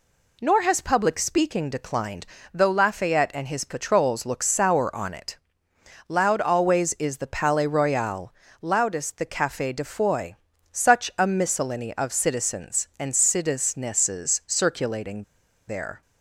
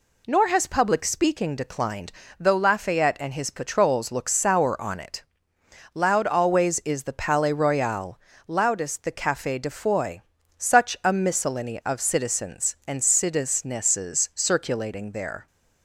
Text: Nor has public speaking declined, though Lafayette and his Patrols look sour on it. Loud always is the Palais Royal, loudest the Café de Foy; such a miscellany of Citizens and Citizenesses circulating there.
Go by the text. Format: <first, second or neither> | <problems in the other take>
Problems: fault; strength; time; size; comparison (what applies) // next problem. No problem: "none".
second | pauses between "circulating" and "there"; at 15.2 s; 0.45 s long